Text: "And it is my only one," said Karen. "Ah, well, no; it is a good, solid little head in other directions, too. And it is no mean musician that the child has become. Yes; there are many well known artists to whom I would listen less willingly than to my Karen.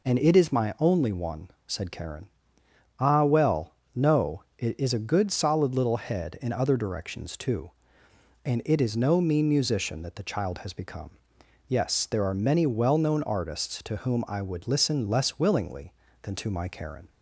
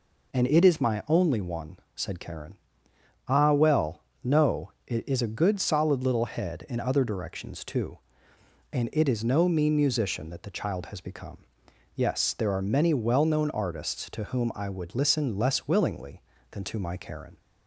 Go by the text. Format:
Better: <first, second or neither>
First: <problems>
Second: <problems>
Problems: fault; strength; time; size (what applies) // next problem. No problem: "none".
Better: neither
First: none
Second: none